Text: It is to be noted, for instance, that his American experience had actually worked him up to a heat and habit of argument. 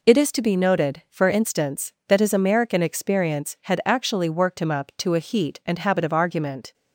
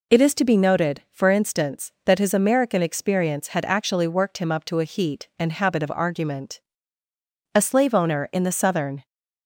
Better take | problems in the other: first | goes on to say "A slave owner in the Southern"; from 7.5 s on; 1.5 s long

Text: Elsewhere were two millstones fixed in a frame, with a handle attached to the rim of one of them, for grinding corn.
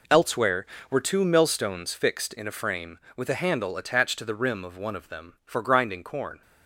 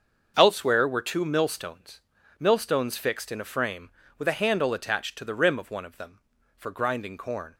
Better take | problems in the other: first | starts louder than the rest; until 1.3 s; 6.5 dB // says "millstones" twice; at 2.4 s

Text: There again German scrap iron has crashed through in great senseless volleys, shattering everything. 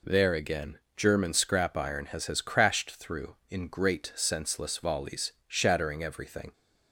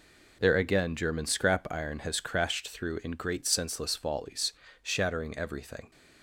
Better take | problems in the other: second | pauses between "again" and "German"; slight; at 0.7 s; 0.20 s long // says "has" twice; at 2.2 s

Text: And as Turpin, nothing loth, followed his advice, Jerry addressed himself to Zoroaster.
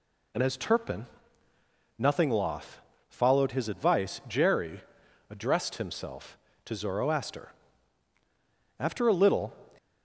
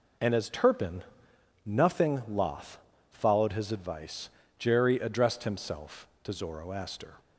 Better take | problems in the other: second | pauses between "Jerry" and "addressed"; noticeable; at 4.8 s; 0.48 s long // goes on to say "After a little"; noticeable; from 8.7 s on; 0.74 s long

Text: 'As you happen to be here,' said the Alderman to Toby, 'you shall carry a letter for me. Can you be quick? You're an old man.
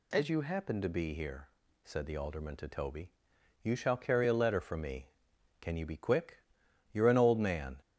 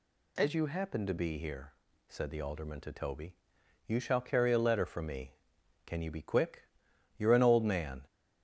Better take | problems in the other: neither | none

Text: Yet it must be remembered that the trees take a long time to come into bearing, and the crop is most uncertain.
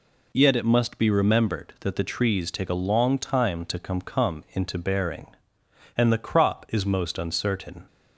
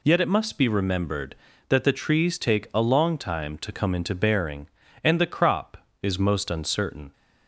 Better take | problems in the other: second | says "come" twice; at 4.0 s

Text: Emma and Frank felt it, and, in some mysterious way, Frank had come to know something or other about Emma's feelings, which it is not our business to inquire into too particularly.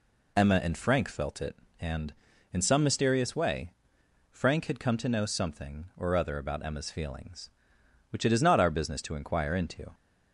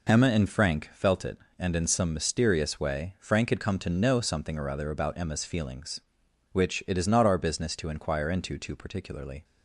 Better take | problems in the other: second | stops before "too particularly"; at 9.9 s

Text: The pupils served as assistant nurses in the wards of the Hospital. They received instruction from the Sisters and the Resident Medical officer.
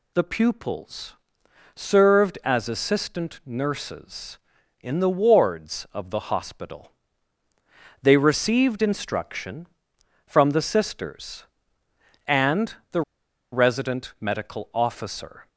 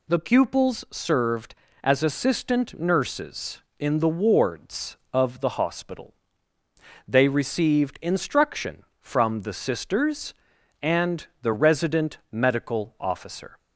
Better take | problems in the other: second | pauses between "pupils" and "served"; noticeable; at 1.1 s; 0.60 s long // pauses between "and" and "the"; slight; at 12.7 s; 0.18 s long // pauses between "the" and "Resident"; noticeable; at 13.0 s; 0.51 s long

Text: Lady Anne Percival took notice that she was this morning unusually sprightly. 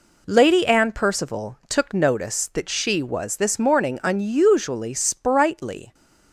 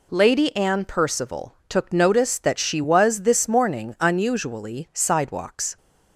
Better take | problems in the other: first | says "sidewalks" for "sprightly"; at 4.9 s

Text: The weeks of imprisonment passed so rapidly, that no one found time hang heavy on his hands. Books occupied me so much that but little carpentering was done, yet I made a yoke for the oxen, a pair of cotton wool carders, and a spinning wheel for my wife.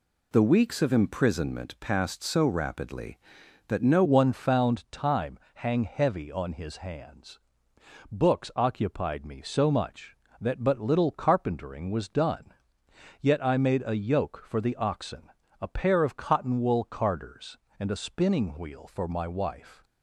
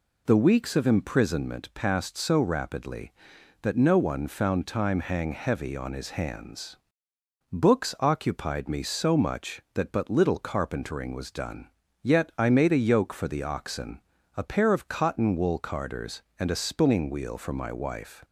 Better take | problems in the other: second | changes voice at "one"; from 4.0 s on; 15.8 s long // pauses between "time" and "hang"; slight; at 5.3 s; 0.16 s long

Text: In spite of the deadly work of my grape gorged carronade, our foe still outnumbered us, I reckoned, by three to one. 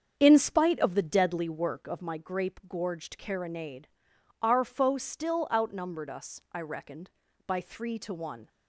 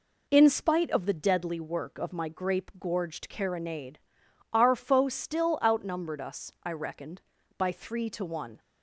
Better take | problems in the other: second | starts louder than the rest; until 1.9 s; 7 dB

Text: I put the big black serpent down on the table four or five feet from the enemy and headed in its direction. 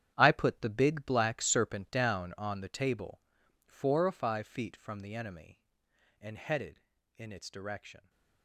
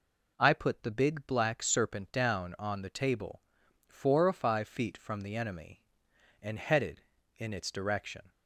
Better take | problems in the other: second | gets quieter; strong; throughout; 13 dB // pauses between "table" and "four"; at 3.2 s; 0.44 s long; also in the second

